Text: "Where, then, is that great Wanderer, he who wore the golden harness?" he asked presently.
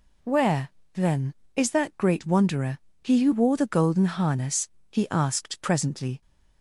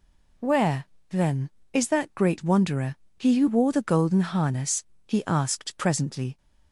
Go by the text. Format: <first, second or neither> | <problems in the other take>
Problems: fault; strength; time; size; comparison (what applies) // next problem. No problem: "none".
neither | none